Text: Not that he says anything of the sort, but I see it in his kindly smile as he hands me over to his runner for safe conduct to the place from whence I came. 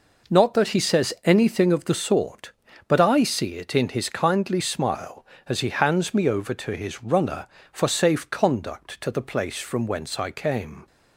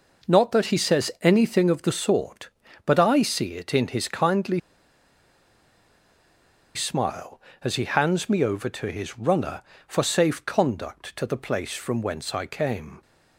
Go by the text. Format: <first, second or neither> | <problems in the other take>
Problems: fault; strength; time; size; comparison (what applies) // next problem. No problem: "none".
first | pauses between "kindly" and "smile"; strong; at 4.6 s; 2.1 s long